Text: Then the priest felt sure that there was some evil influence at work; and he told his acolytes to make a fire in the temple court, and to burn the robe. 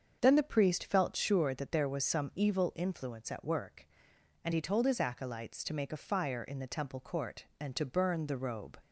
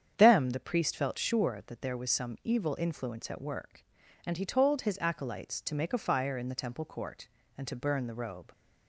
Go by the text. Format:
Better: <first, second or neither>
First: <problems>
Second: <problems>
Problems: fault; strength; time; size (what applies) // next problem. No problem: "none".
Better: first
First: starts louder than the rest; until 1.2 s; 7 dB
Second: starts louder than the rest; strong; until 1.1 s; 8 dB // says "Them" for "Then"; at 0.1 s